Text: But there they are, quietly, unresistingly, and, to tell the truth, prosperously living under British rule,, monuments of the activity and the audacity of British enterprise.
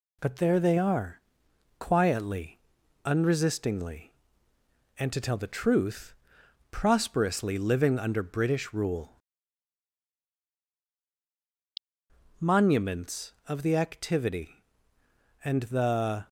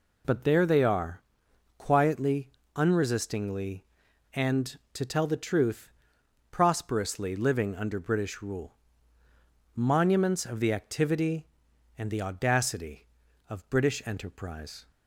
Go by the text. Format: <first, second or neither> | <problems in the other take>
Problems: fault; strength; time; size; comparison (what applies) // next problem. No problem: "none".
second | stops before "audacity of British enterprise"; at 16.2 s